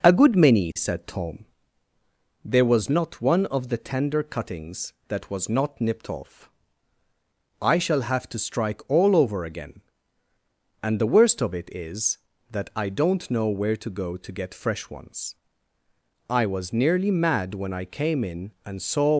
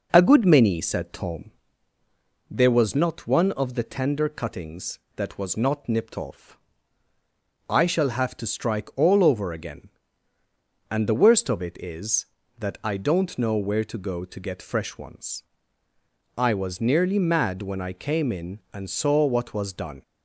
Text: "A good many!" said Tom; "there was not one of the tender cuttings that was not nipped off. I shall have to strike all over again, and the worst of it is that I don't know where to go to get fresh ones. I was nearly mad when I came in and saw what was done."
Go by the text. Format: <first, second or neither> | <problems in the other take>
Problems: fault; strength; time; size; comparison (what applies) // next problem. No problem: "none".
second | stops before "what was done"; at 19.1 s